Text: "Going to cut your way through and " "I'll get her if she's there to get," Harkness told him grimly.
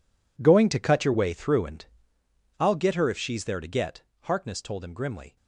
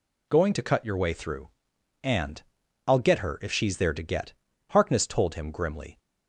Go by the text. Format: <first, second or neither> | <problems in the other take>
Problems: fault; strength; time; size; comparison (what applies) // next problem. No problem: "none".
second | gets quieter; strong; throughout; 12 dB